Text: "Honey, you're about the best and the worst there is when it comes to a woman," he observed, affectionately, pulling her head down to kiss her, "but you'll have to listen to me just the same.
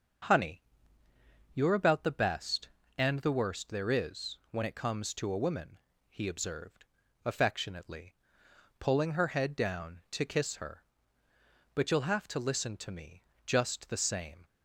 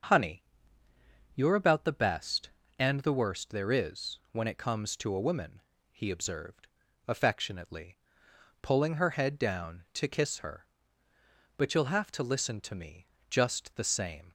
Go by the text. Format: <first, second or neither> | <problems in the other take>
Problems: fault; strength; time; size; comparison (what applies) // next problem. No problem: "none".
neither | starts louder than the rest; the same in both // pauses between "me" and "just"; slight; the same in both